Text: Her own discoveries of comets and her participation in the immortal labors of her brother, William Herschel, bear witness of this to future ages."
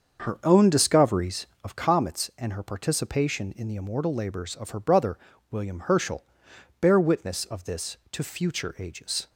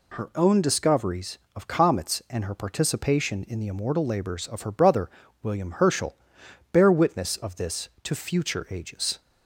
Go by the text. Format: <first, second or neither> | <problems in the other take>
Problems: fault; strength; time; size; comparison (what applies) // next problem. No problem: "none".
second | starts louder than the rest; until 1.8 s; 6.5 dB